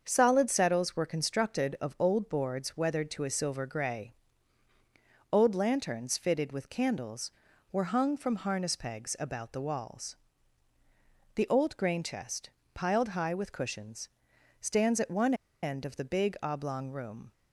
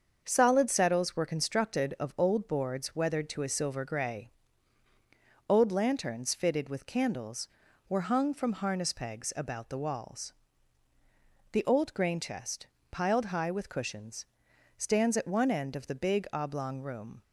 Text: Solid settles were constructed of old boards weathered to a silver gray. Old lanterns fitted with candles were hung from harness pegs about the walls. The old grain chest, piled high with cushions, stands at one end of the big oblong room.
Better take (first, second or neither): second